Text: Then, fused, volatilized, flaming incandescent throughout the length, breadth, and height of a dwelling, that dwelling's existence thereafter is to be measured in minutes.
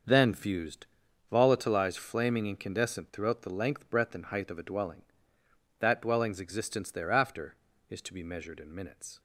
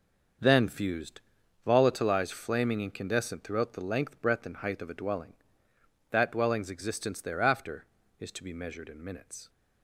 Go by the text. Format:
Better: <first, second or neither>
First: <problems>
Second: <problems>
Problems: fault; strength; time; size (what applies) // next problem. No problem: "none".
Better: neither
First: starts louder than the rest; until 1.5 s; 6.5 dB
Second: starts louder than the rest; until 1.8 s; 6.5 dB